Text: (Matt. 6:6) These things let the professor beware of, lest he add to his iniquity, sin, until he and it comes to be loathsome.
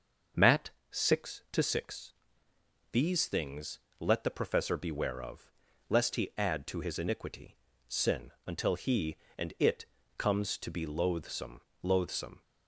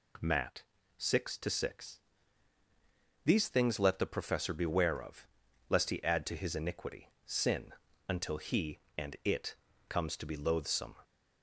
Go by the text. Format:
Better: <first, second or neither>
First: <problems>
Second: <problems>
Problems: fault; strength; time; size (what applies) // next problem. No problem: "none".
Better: second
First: starts louder than the rest; until 1.7 s; 6.5 dB // pauses between "things" and "let"; slight; at 3.7 s; 0.22 s long // pauses between "it" and "comes"; slight; at 9.8 s; 0.32 s long // says "loathsome" twice; at 11.8 s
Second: pauses between "it" and "comes"; slight; at 9.5 s; 0.34 s long